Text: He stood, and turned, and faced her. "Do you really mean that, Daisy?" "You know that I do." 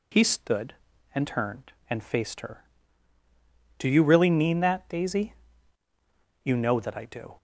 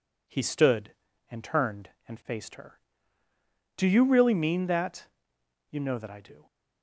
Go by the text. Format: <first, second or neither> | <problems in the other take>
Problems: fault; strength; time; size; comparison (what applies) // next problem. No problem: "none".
first | skips "Daisy"; at 5.3 s